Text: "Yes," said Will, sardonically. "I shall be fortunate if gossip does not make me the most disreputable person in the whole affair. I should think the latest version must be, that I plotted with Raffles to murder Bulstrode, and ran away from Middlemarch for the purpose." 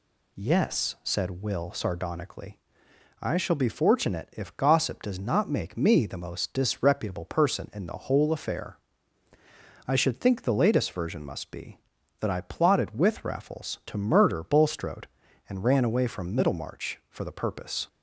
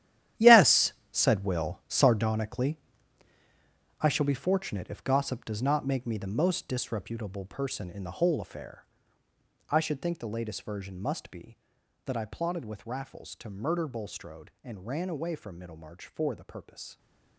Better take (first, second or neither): first